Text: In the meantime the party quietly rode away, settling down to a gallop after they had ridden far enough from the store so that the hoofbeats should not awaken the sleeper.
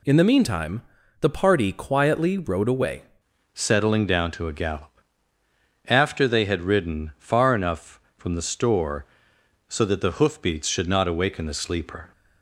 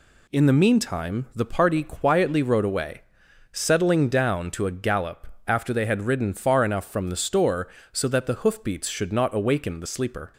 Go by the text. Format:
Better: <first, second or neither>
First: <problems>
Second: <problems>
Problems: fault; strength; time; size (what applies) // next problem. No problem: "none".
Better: second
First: pauses between "meantime" and "the"; at 0.8 s; 0.40 s long // changes voice at "settling"; from 3.5 s on; 8.6 s long // pauses between "gallop" and "after"; noticeable; at 4.9 s; 0.92 s long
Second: pauses between "gallop" and "after"; slight; at 5.2 s; 0.22 s long